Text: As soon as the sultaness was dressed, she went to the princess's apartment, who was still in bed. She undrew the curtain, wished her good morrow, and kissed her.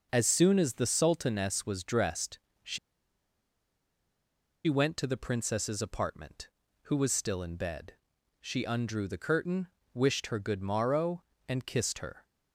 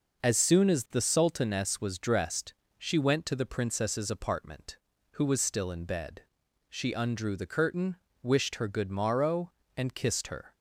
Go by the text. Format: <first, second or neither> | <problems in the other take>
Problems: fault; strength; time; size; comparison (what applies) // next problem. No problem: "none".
second | pauses between "she" and "went"; strong; at 2.7 s; 1.8 s long